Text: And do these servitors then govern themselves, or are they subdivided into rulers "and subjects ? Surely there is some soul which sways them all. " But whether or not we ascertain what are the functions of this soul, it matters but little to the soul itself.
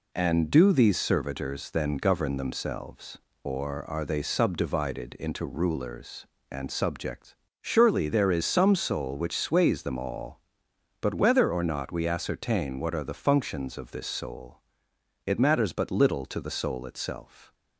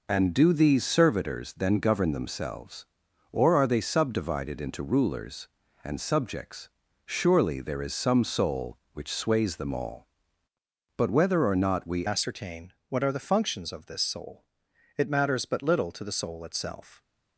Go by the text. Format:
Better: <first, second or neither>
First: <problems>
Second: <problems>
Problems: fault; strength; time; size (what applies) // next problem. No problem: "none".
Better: first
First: none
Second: changes voice at "ascertain"; from 12.0 s on; 5.0 s long // pauses between "ascertain" and "what"; slight; at 12.7 s; 0.16 s long